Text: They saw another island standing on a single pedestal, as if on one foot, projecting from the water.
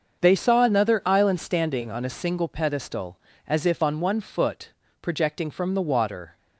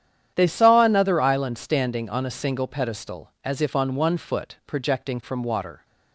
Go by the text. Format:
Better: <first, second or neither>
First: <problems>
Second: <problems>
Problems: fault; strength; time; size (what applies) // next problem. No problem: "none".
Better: first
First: starts louder than the rest; until 1.2 s; 6.5 dB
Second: starts louder than the rest; strong; until 1.3 s; 9.5 dB // skips "the"; at 5.4 s